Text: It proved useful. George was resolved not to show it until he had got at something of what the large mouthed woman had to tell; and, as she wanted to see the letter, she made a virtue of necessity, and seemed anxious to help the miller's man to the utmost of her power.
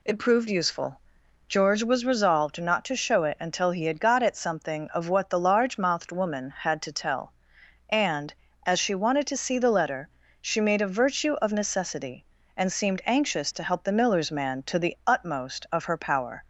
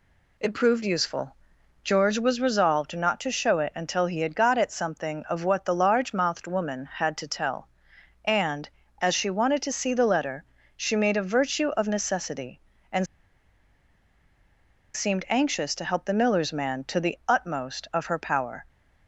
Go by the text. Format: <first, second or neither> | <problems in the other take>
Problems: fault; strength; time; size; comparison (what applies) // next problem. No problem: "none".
first | pauses between "and" and "seemed"; strong; at 13.0 s; 1.8 s long